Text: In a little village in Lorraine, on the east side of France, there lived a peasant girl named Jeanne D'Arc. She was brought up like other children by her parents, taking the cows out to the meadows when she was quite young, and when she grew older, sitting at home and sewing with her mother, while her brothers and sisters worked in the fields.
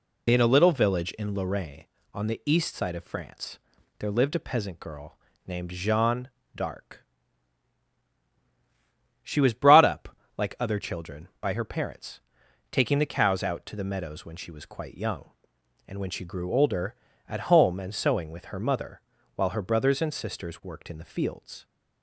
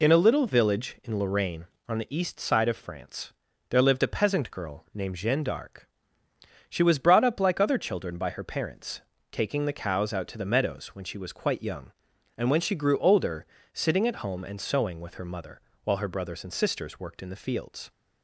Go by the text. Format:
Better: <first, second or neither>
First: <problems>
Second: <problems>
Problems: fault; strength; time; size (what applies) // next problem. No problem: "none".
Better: second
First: pauses between "girl" and "named"; slight; at 5.1 s; 0.30 s long // pauses between "Jeanne" and "D'Arc"; slight; at 6.2 s; 0.26 s long // pauses between "up" and "like"; slight; at 10.1 s; 0.22 s long // skips "sitting"; at 17.0 s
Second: none